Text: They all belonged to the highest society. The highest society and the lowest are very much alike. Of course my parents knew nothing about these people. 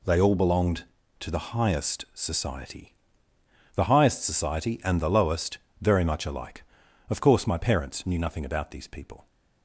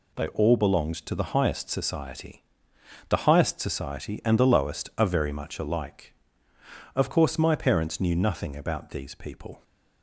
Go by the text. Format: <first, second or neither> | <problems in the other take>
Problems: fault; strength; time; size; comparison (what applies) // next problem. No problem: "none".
second | skips "are"; at 5.6 s